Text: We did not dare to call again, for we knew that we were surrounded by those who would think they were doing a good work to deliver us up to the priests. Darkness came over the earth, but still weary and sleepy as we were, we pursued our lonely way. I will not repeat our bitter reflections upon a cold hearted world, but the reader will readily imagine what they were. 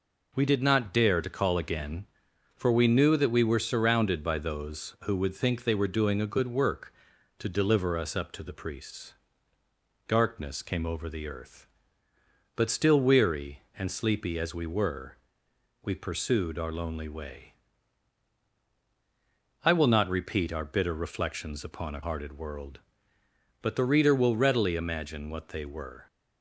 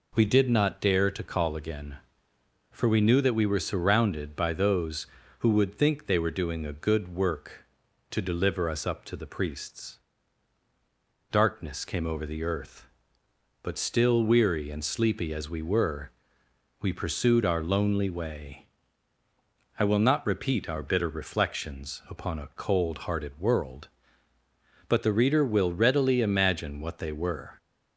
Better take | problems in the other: second | skips "cold"; at 22.0 s

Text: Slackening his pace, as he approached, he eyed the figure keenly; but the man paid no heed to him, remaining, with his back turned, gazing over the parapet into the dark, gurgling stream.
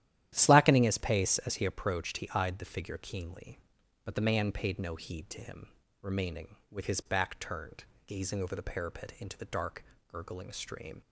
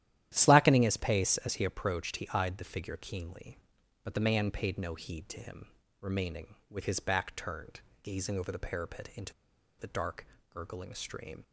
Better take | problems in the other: first | starts louder than the rest; strong; until 1.3 s; 12 dB; strong in the first // pauses between "into" and "the"; noticeable; at 9.3 s; 0.47 s long

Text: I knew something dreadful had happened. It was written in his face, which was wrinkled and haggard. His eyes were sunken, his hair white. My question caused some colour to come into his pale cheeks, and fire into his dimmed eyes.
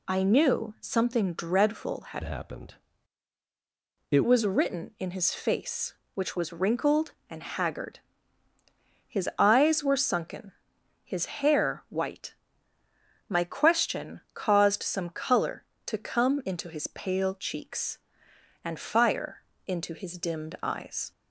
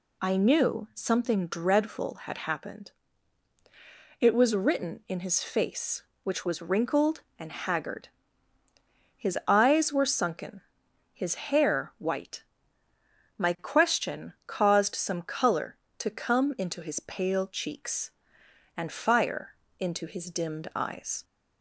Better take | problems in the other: second | changes voice from "happened" to "It"; from 2.2 to 4.2 s; 2.0 s long // pauses between "fire" and "into"; slight; at 19.4 s; 0.24 s long; slight in the second

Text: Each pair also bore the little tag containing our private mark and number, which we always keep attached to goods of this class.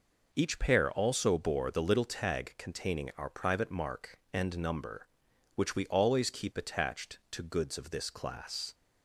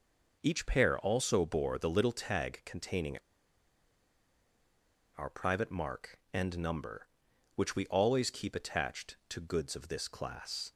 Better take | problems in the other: first | pauses between "containing" and "our"; strong; at 3.1 s; 2.0 s long

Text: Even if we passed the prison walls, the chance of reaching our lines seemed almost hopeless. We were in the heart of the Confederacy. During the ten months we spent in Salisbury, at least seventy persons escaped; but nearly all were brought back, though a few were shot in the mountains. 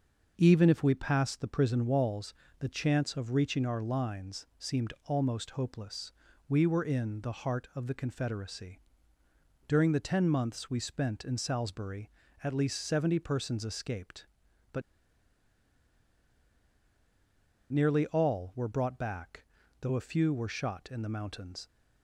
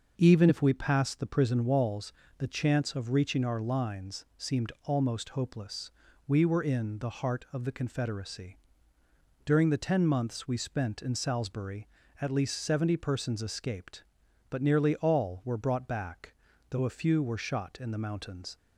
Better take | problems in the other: second | starts louder than the rest; until 1.3 s; 6 dB // pauses between "but" and "nearly"; strong; at 14.8 s; 2.8 s long

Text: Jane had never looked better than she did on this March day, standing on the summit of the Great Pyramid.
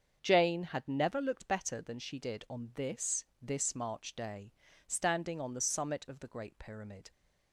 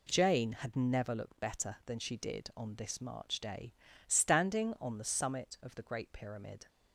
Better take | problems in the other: second | starts louder than the rest; until 1.2 s; 7 dB // says "this" twice; at 3.4 s

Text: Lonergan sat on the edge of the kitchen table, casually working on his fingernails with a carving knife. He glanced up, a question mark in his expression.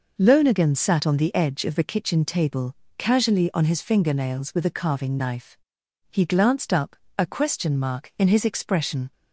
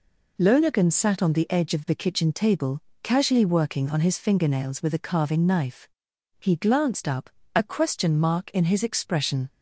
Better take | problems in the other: second | skips "working"; at 3.5 s

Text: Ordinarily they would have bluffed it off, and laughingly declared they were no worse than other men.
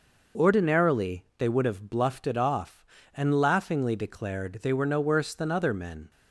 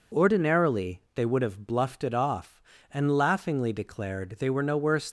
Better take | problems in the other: first | stops before "than other men"; at 5.0 s

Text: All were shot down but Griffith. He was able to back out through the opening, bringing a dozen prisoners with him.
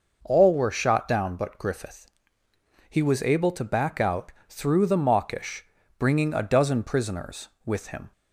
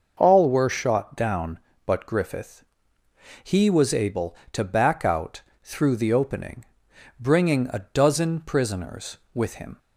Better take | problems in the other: second | pauses between "out" and "through"; slight; at 4.3 s; 0.18 s long; slight in the second // says "mawkish" for "opening"; at 4.9 s

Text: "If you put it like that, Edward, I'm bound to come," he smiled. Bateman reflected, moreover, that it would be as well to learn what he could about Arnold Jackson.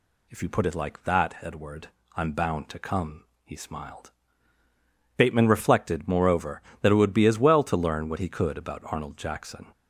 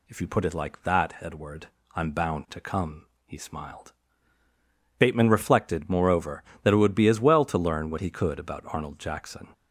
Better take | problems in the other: neither | none

